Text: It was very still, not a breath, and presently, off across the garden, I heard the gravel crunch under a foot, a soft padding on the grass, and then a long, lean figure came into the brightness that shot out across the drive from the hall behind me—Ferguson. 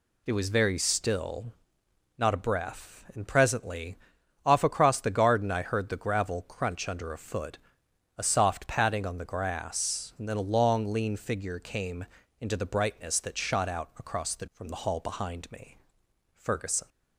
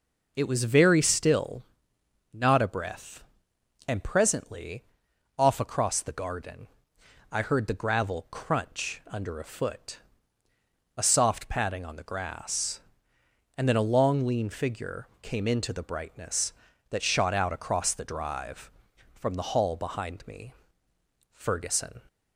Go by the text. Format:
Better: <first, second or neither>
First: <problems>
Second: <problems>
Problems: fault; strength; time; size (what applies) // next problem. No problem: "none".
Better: second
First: pauses between "came" and "into"; slight; at 12.0 s; 0.34 s long // skips "drive"; at 14.4 s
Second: none